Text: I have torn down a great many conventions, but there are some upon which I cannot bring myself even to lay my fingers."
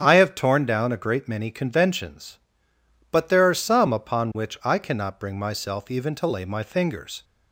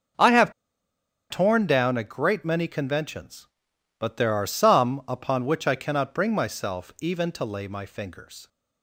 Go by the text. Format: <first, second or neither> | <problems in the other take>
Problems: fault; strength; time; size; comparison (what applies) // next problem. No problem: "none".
first | starts louder than the rest; until 1.9 s; 6.5 dB; strong in the first // pauses between "have" and "torn"; noticeable; at 0.5 s; 0.77 s long